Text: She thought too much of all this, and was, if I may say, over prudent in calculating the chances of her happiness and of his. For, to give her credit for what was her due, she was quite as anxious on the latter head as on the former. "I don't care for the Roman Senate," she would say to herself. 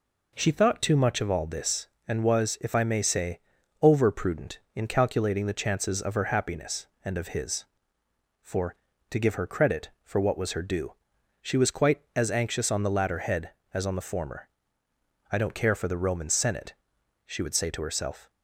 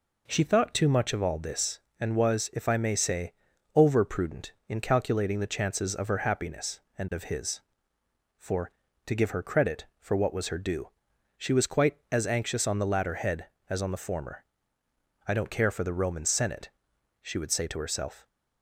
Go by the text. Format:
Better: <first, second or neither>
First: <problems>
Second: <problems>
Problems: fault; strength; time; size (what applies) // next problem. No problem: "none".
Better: neither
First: none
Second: none